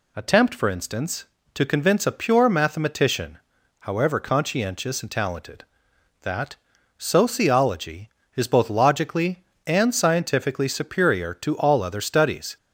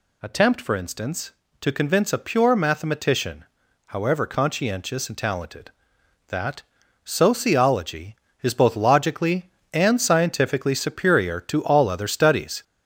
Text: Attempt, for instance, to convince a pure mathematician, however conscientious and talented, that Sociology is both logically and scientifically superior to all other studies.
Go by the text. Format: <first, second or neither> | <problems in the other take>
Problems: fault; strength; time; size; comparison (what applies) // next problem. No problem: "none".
first | gets louder; noticeable; throughout; 4 dB // pauses between "that" and "Sociology"; at 6.6 s; 0.42 s long; also in the first